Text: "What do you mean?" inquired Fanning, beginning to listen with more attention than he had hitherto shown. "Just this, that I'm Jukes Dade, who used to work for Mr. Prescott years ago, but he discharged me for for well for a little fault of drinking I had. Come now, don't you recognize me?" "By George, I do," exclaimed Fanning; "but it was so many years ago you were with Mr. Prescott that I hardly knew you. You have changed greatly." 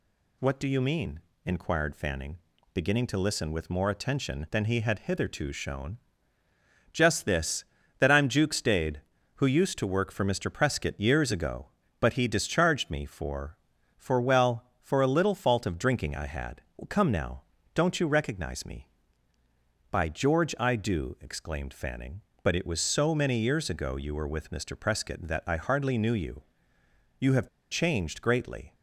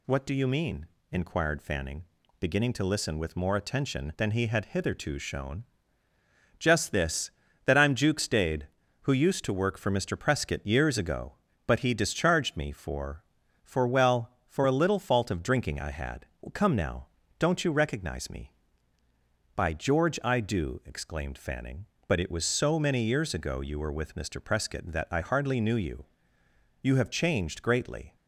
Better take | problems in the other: second | pauses between "have" and "changed"; slight; at 27.4 s; 0.22 s long

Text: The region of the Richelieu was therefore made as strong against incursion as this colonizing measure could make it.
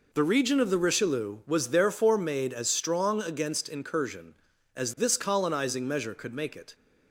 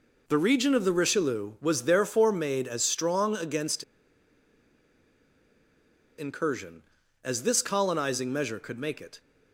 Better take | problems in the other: first | pauses between "against" and "incursion"; strong; at 3.8 s; 2.3 s long

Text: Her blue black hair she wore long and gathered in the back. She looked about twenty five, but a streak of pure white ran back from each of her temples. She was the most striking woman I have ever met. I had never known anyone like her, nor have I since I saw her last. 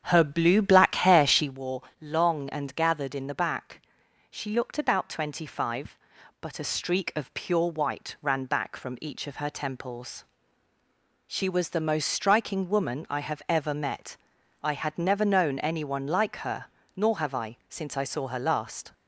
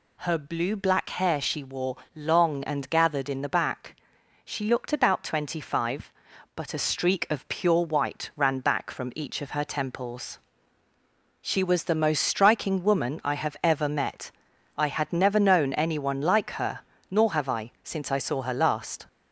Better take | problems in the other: second | starts louder than the rest; strong; until 1.6 s; 8 dB // pauses between "wore" and "long"; slight; at 1.8 s; 0.18 s long; slight in the second

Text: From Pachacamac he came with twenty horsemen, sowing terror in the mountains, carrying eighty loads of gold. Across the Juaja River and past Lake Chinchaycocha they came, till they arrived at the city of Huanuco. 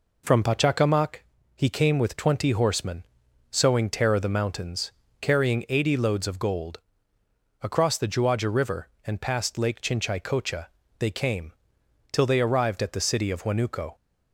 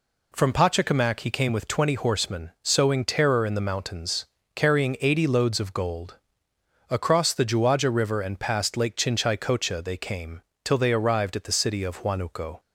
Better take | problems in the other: second | pauses between "Pachacamac" and "he"; at 1.1 s; 0.38 s long // skips "in"; at 4.1 s // pauses between "Chinchaycocha" and "they"; slight; at 10.6 s; 0.32 s long

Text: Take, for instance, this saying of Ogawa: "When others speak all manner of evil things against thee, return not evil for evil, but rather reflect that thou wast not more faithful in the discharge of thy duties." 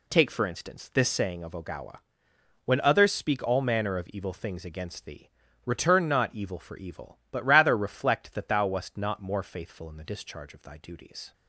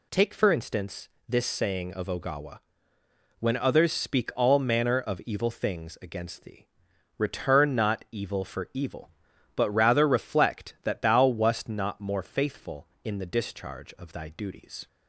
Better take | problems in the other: neither | none

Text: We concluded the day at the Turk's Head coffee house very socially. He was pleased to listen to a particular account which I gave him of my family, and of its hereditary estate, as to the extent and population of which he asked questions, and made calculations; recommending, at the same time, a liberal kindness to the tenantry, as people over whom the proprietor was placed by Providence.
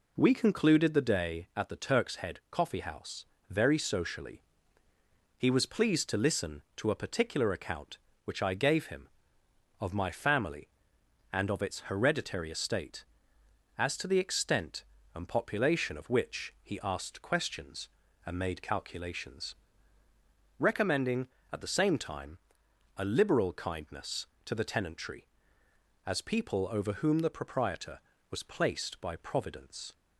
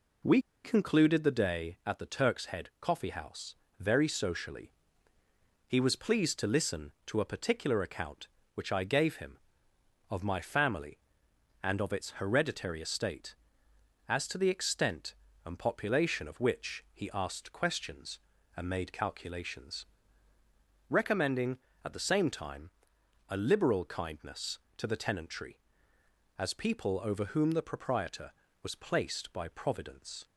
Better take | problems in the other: first | pauses between "We" and "concluded"; slight; at 0.4 s; 0.23 s long // pauses between "house" and "very"; slight; at 3.5 s; 0.24 s long; slight in the first

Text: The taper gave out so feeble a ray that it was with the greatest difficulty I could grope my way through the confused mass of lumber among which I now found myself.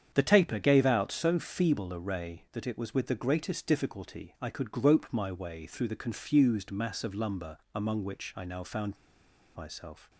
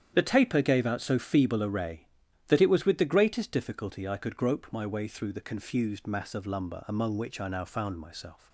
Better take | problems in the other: second | starts louder than the rest; strong; until 1.1 s; 8 dB; strong in the second // pauses between "lumber" and "among"; slight; at 7.5 s; 0.18 s long // pauses between "found" and "myself"; noticeable; at 8.9 s; 0.59 s long

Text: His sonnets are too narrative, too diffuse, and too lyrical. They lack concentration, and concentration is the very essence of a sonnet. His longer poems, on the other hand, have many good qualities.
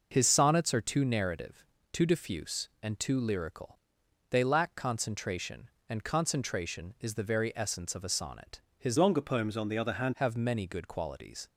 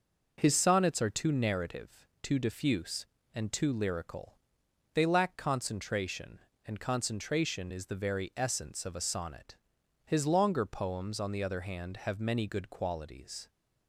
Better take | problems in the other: second | changes voice from "longer" to "hand"; from 8.9 to 10.1 s; 1.2 s long

